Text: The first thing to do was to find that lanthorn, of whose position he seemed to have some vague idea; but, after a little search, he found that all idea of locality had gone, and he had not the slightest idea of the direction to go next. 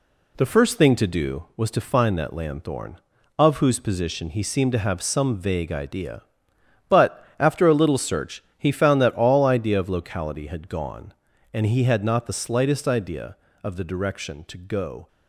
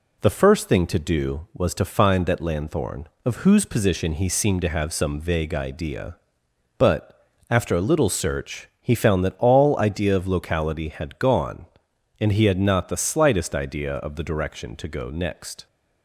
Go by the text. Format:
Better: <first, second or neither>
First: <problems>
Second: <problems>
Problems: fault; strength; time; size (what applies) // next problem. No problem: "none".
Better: second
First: stops before "next"; at 15.0 s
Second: none